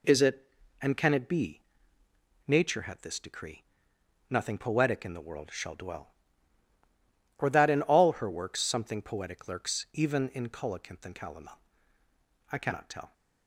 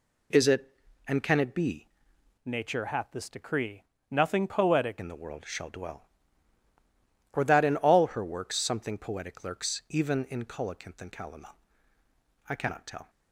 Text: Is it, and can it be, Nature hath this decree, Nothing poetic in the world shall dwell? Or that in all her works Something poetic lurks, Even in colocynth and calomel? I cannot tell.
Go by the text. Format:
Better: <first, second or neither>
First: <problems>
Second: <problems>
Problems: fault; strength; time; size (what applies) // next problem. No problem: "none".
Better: first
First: none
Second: changes voice from "Nature" to "poetic"; from 2.4 to 5.0 s; 2.6 s long